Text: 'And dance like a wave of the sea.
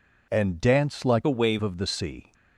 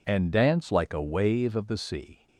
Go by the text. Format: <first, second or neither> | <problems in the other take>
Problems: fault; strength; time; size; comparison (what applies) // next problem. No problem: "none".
second | changes voice from "a" to "wave"; from 1.2 to 1.5 s; 0.3 s long